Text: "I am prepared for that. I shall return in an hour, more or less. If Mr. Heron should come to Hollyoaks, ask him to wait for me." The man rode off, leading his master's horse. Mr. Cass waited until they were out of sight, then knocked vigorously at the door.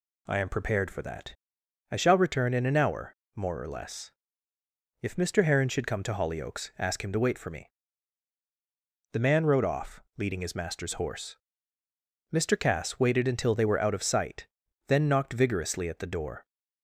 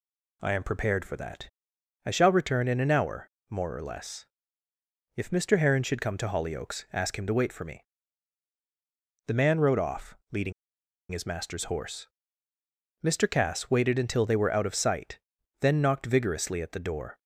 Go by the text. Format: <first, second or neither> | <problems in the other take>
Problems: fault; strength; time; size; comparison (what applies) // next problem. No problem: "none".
first | pauses between "leading" and "his"; noticeable; at 10.5 s; 0.59 s long